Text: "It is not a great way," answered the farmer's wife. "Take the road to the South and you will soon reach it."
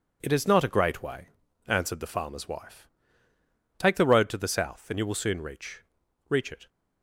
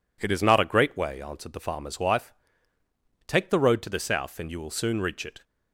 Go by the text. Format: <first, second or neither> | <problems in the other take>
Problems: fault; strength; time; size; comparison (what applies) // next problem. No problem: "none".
second | says "reach" twice; at 6.2 s